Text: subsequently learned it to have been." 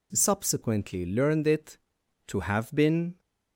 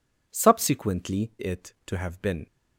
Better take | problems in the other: first | skips "learned"; at 1.3 s

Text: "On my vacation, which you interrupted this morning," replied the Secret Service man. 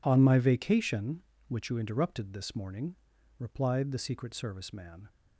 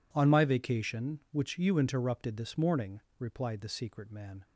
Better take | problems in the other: first | skips "Service"; at 4.1 s

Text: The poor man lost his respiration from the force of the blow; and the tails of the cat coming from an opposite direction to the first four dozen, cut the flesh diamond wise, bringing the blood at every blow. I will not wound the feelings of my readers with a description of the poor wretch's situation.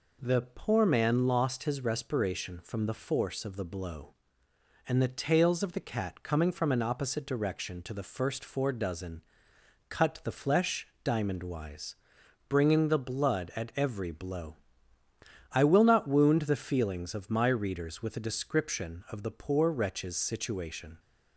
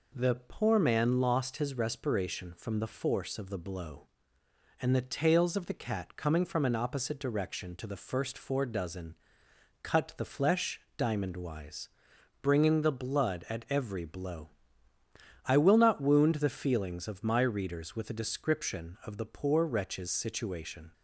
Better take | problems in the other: neither | pauses between "flesh" and "diamond"; slight; the same in both

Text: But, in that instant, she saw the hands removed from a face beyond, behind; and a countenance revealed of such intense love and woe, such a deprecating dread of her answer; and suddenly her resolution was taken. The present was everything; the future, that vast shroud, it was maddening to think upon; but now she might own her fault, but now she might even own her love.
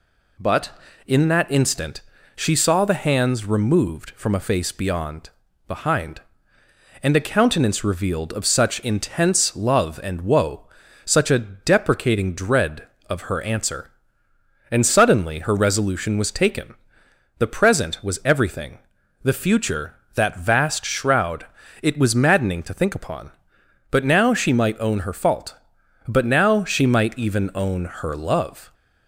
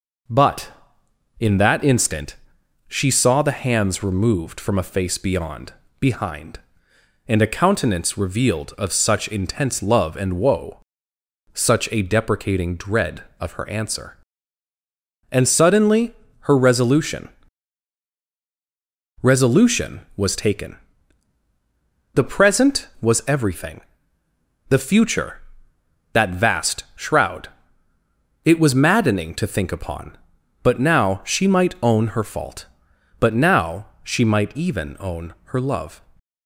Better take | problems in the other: first | pauses between "suddenly" and "her"; slight; at 16.1 s; 0.24 s long // says "resolution" twice; at 19.2 s // pauses between "now" and "she"; slight; at 33.8 s; 0.16 s long

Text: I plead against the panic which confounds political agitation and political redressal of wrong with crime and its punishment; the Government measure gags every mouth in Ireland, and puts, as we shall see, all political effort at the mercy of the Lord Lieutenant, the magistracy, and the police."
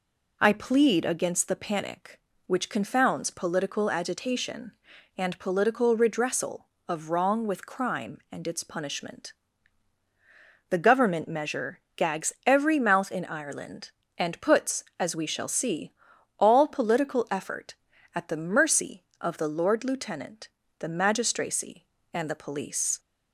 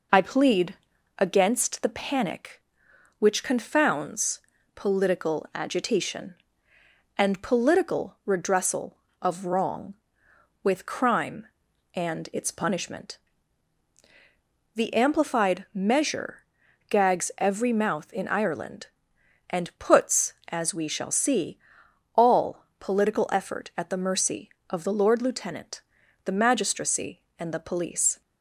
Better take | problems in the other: first | pauses between "plead" and "against"; at 0.7 s; 0.42 s long // pauses between "confounds" and "political"; slight; at 4.3 s; 0.34 s long // says "Amplified" for "Government"; at 14.9 s // pauses between "measure" and "gags"; noticeable; at 16.3 s; 0.49 s long; slight in the first // pauses between "all" and "political"; slight; at 22.6 s; 0.16 s long

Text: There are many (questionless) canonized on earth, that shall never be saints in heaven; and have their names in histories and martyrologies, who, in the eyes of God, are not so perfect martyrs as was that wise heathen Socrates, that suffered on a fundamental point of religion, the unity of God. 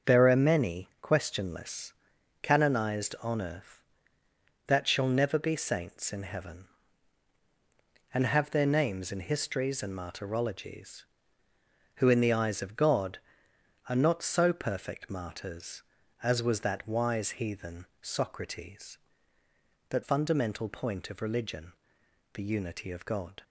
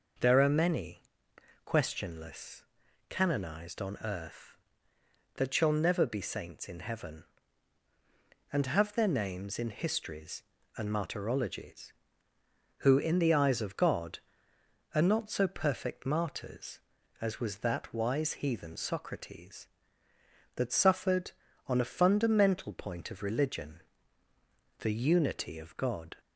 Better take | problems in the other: second | starts louder than the rest; until 1.2 s; 6.5 dB // pauses between "heathen" and "Socrates"; slight; at 17.8 s; 0.16 s long // skips "suffered on a"; at 20.0 s

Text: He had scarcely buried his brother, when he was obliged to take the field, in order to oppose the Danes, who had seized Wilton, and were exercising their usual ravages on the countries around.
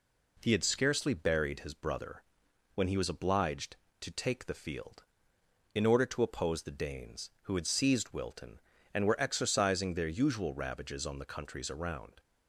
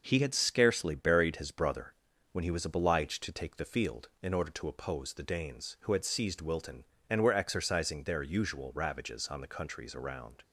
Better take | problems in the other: neither | none

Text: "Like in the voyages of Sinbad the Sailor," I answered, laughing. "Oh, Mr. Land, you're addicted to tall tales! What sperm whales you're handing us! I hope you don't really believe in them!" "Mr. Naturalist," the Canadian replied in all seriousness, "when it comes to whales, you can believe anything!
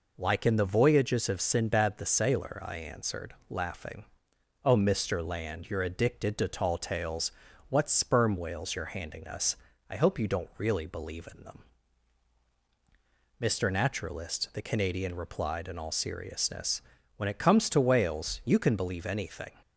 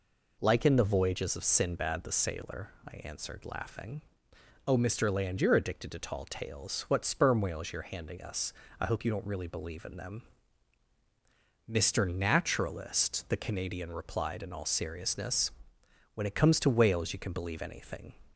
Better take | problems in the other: neither | none

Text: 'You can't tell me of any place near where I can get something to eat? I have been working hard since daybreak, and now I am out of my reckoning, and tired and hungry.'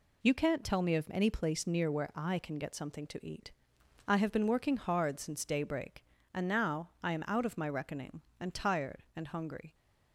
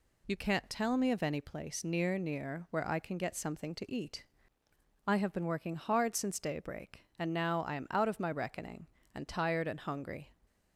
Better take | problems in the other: first | says "near" twice; at 2.1 s

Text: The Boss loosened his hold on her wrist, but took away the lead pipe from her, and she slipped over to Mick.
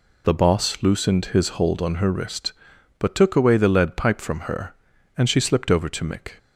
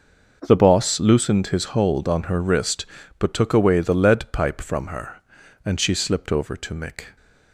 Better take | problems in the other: neither | none

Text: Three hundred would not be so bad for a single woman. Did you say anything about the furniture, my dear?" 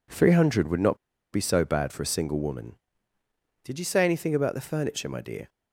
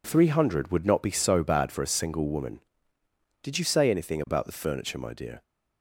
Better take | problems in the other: second | pauses between "not" and "be"; slight; at 0.9 s; 0.35 s long

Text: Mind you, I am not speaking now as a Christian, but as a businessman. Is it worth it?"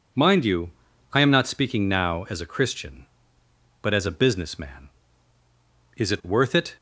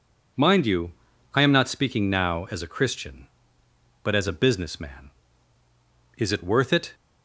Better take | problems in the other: neither | none

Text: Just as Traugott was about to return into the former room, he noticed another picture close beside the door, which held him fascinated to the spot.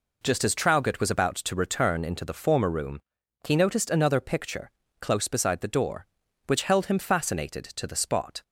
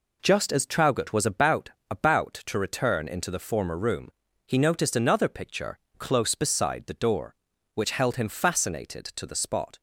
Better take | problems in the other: first | says "about" twice; at 1.8 s // pauses between "picture" and "close"; slight; at 5.7 s; 0.20 s long; slight in the first

